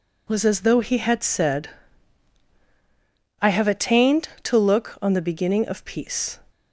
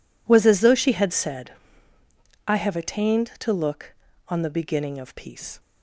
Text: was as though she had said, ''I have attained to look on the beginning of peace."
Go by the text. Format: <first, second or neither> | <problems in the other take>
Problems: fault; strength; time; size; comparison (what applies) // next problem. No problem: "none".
second | says "he" for "she"; at 0.8 s